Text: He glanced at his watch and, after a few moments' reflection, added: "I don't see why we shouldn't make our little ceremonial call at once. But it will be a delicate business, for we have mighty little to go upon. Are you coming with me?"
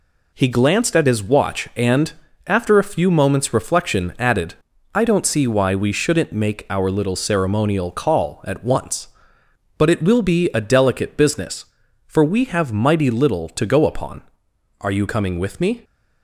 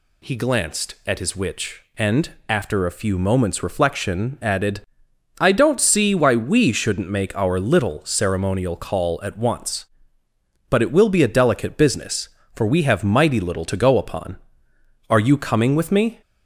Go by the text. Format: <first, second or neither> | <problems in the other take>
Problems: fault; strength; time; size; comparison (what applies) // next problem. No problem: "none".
first | says "witch" for "watch"; at 1.3 s